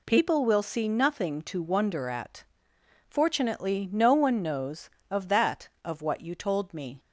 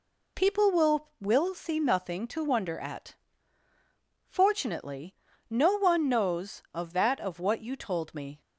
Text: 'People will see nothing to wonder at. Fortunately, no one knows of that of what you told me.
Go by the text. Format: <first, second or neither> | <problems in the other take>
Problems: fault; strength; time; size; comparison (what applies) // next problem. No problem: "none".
first | says "will" twice; at 1.2 s